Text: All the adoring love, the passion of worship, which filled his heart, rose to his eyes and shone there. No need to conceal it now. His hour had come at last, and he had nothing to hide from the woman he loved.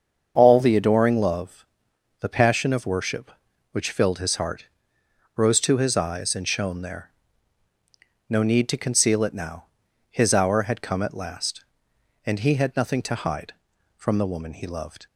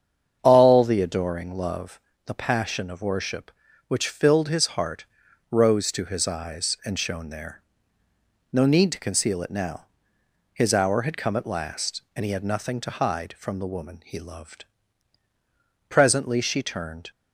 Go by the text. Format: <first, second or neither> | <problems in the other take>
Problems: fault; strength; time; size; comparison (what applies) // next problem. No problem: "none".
first | starts louder than the rest; strong; until 1.4 s; 7.5 dB; also in the first // goes on to say "Presently she turned"; noticeable; from 15.8 s on; 1.2 s long